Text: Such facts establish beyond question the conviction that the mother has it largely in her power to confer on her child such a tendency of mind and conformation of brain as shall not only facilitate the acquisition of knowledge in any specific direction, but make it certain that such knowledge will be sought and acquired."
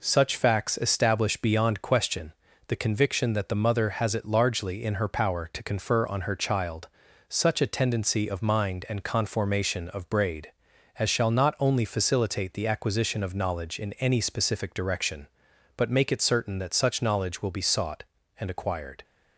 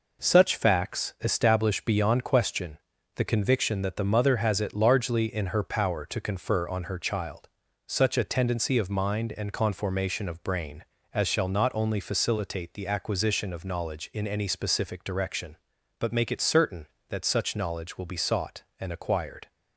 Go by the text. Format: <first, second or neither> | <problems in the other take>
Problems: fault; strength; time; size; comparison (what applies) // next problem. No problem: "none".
second | pauses between "question" and "the"; slight; at 2.3 s; 0.36 s long; also in the second // pauses between "child" and "such"; at 6.8 s; 0.42 s long; also in the second // says "braid" for "brain"; at 10.0 s